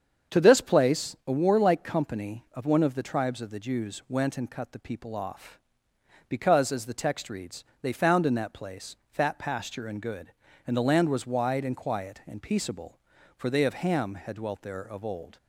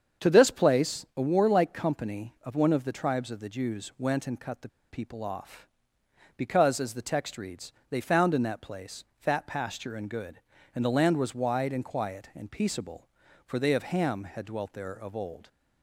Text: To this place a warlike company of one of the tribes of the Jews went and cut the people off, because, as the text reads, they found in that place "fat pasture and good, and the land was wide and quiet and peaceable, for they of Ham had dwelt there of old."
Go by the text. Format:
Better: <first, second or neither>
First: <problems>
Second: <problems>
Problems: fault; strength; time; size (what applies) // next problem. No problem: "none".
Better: first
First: starts louder than the rest; strong; until 1.4 s; 7 dB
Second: starts louder than the rest; strong; until 1.3 s; 7 dB // pauses between "the" and "people"; slight; at 4.6 s; 0.21 s long